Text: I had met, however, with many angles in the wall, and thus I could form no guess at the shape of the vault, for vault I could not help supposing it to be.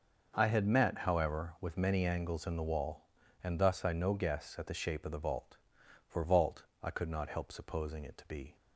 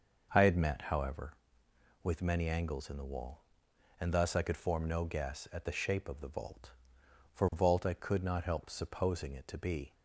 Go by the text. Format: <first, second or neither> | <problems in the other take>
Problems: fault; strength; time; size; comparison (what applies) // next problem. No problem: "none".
second | skips "could form"; at 3.9 s // pauses between "vault" and "I"; slight; at 6.6 s; 0.18 s long